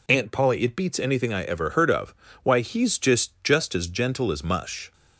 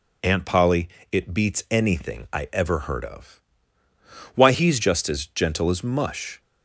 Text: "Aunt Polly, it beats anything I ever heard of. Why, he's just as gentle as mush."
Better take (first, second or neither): second